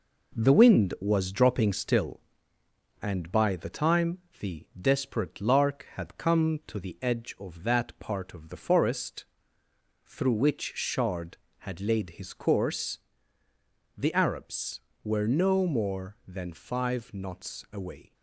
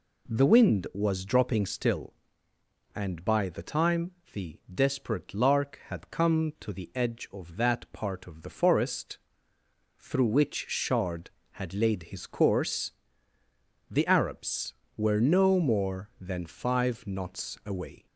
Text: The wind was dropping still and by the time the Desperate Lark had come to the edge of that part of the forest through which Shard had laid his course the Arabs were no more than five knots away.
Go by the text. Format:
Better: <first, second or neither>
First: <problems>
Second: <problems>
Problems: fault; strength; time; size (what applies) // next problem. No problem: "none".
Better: second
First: gets quieter; noticeable; throughout; 5 dB // pauses between "time" and "the"; slight; at 4.1 s; 0.20 s long // pauses between "forest" and "through"; noticeable; at 9.2 s; 0.78 s long // pauses between "course" and "the"; noticeable; at 12.9 s; 0.98 s long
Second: pauses between "time" and "the"; slight; at 4.1 s; 0.20 s long // pauses between "forest" and "through"; noticeable; at 9.1 s; 0.78 s long // pauses between "course" and "the"; noticeable; at 12.9 s; 0.98 s long